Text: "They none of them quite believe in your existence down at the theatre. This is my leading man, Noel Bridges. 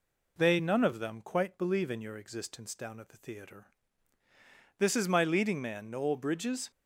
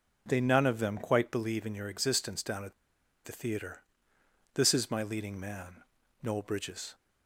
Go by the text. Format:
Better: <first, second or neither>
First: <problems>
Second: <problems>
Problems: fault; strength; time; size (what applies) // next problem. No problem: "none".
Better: first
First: none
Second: pauses between "at" and "the"; noticeable; at 2.7 s; 0.52 s long